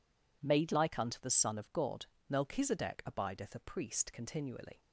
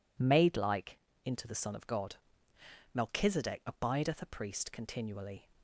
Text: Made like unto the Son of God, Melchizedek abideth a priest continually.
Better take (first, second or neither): first